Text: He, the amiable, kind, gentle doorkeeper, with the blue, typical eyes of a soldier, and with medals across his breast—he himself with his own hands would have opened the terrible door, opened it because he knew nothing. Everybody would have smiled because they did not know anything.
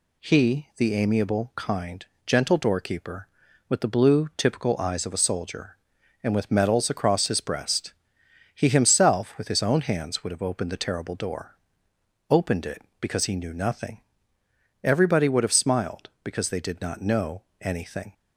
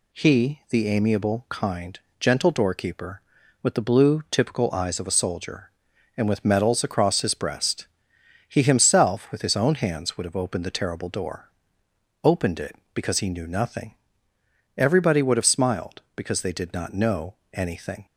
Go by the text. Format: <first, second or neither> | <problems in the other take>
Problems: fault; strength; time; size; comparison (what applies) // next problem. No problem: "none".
neither | pauses between "know" and "anything"; slight; the same in both